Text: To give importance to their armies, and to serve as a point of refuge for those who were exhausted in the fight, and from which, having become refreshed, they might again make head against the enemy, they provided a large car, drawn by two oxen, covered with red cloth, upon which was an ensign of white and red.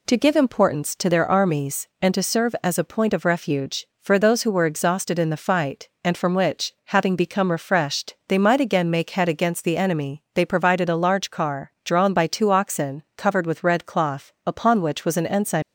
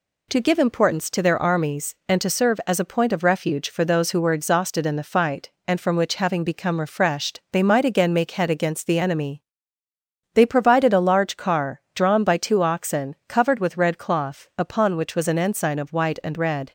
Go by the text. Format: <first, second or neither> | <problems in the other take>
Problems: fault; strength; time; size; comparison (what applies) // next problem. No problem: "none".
second | stops before "of white and red"; at 15.6 s